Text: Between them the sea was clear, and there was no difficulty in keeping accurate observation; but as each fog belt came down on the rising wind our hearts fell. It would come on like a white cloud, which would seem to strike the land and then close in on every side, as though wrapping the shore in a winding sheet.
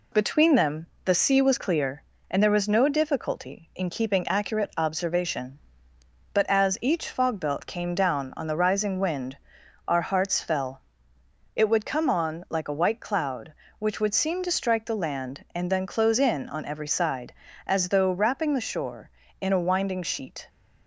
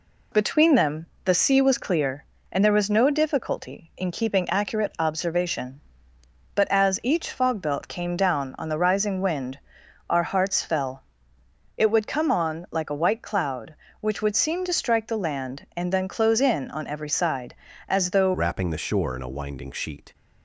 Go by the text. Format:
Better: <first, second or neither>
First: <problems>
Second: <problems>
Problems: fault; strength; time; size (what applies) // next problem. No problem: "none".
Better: first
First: pauses between "them" and "the"; slight; at 0.8 s; 0.18 s long // pauses between "wind" and "our"; noticeable; at 9.3 s; 0.50 s long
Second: pauses between "them" and "the"; slight; at 1.0 s; 0.18 s long // pauses between "wind" and "our"; noticeable; at 9.5 s; 0.50 s long // changes voice at "wrapping"; from 18.3 s on; 1.8 s long